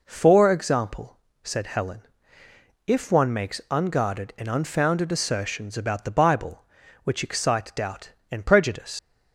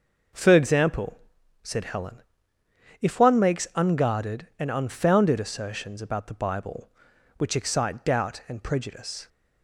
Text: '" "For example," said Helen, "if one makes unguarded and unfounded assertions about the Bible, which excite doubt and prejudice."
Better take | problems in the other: second | leaves "prejudice" unfinished; at 8.9 s; 100 ms

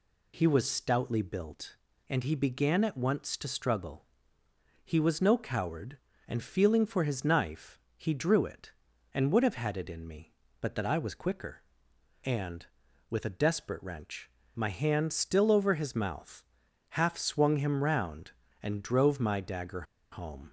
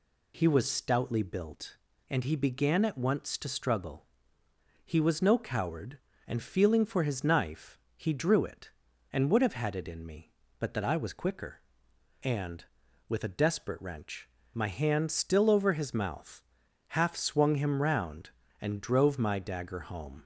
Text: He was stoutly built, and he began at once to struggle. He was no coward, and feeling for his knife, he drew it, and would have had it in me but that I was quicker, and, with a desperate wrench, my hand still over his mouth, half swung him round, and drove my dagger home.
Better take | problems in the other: second | pauses between "dagger" and "home"; slight; at 19.8 s; 0.29 s long

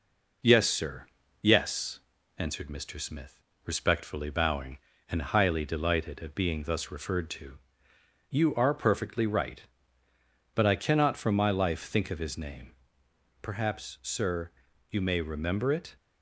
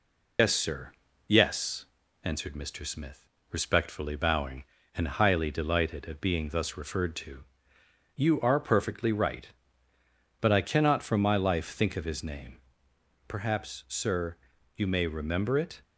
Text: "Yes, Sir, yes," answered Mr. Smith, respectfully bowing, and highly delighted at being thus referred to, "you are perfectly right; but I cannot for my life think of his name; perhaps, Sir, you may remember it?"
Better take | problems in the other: first | loses the start of "Yes"; at 0.3 s; 120 ms

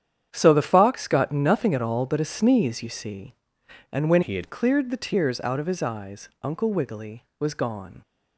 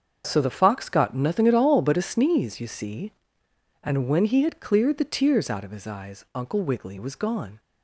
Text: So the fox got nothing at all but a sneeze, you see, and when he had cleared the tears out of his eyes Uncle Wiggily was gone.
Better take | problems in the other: second | starts louder than the rest; strong; until 1.3 s; 9 dB; also in the second // changes voice from "he" to "had"; from 4.2 to 4.4 s; 0.2 s long // pauses between "eyes" and "Uncle"; slight; at 6.2 s; 0.16 s long

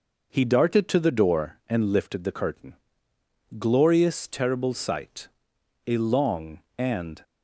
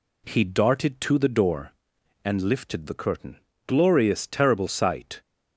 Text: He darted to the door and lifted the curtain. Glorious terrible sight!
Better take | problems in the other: second | goes on to say "A long and"; from 5.8 s on; 1.3 s long

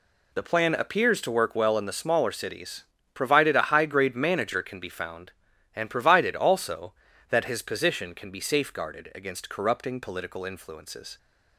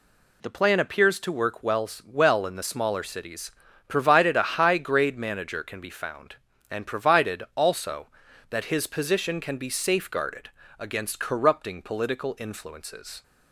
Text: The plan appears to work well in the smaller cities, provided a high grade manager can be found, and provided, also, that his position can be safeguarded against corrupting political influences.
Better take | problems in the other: first | says "well" twice; at 2.0 s // pauses between "safeguarded" and "against"; slight; at 10.4 s; 0.30 s long

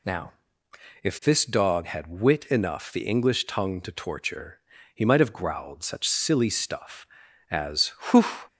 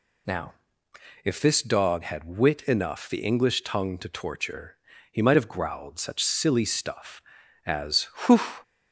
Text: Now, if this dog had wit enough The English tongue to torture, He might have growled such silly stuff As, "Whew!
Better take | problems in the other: neither | none

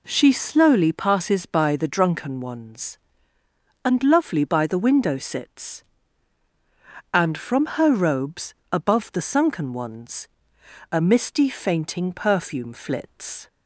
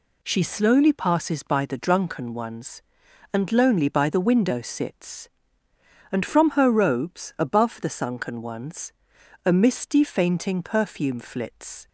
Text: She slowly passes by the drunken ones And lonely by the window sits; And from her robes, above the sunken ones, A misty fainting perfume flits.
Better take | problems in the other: second | says "lovely" for "lonely"; at 4.0 s

